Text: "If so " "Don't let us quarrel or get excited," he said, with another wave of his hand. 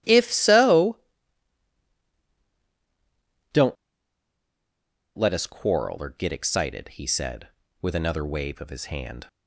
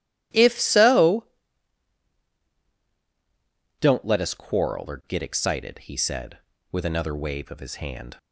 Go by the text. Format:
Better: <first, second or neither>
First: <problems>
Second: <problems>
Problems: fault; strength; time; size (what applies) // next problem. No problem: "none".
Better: second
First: starts louder than the rest; strong; until 1.9 s; 12 dB // pauses between "Don't" and "let"; strong; at 3.7 s; 1.4 s long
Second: starts louder than the rest; strong; until 2.2 s; 11.5 dB